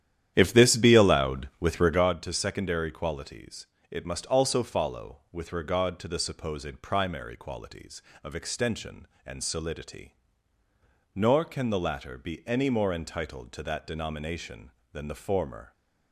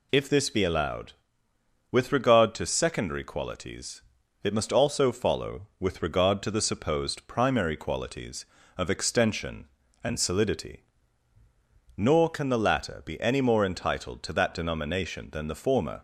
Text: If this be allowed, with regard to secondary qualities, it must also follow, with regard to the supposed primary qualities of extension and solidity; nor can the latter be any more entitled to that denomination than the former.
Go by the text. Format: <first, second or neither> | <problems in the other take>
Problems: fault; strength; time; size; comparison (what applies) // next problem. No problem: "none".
second | starts louder than the rest; strong; until 2.1 s; 10.5 dB